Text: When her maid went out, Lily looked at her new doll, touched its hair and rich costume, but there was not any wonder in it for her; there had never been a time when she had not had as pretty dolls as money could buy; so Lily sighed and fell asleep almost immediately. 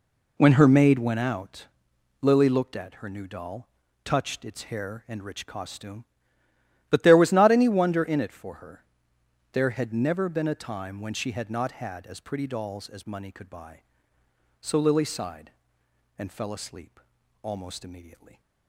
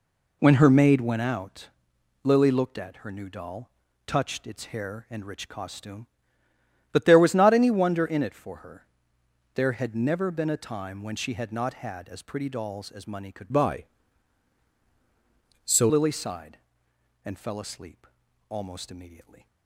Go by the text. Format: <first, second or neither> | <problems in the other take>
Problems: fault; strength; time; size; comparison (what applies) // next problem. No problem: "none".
first | changes voice from "buy" to "so"; from 13.4 to 15.8 s; 2.4 s long // pauses between "asleep" and "almost"; at 18.0 s; 0.40 s long; also in the first